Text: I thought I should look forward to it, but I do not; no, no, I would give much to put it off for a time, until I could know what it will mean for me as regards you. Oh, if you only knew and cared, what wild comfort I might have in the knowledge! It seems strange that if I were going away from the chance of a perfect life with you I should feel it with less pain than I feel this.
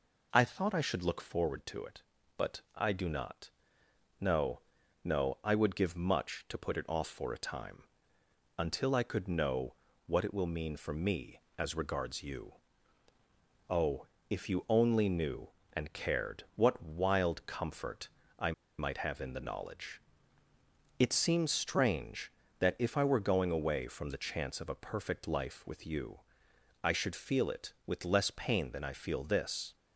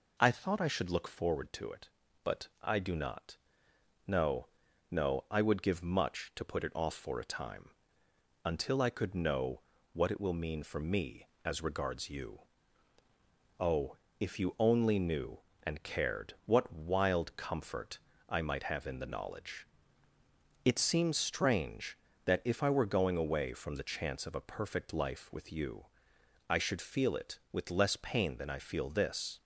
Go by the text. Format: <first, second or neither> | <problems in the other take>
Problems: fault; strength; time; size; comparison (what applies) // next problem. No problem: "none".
second | pauses between "but" and "I"; slight; at 2.6 s; 0.16 s long; slight in the second // pauses between "know" and "what"; slight; at 9.7 s; 0.32 s long; slight in the second // pauses between "comfort" and "I"; slight; at 18.0 s; 0.32 s long; slight in the second // pauses between "I" and "might"; slight; at 18.5 s; 0.26 s long // pauses between "you" and "I"; noticeable; at 26.2 s; 0.64 s long; noticeable in the second